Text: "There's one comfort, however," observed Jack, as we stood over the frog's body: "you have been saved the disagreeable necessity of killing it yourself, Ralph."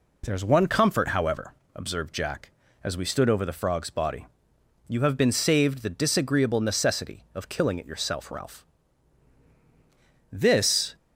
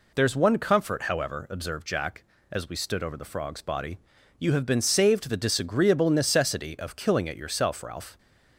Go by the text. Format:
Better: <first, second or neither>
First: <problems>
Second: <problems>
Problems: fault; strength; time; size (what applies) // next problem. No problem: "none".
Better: second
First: goes on to say "This"; noticeable; from 10.3 s on; 0.64 s long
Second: none